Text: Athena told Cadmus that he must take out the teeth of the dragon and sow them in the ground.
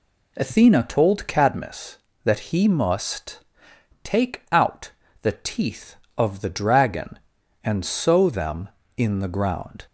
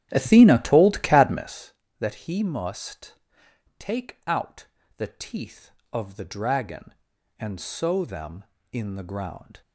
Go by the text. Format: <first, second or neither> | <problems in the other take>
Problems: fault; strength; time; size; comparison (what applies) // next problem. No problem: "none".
first | starts louder than the rest; strong; until 1.7 s; 11 dB // pauses between "must" and "take"; noticeable; at 3.1 s; 0.62 s long; noticeable in the first // pauses between "out" and "the"; slight; at 4.6 s; 0.30 s long; slight in the first